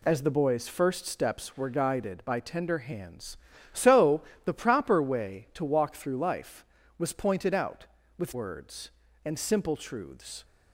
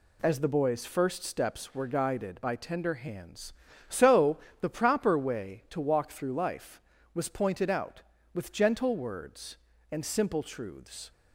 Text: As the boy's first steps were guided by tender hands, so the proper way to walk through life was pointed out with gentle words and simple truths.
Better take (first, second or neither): second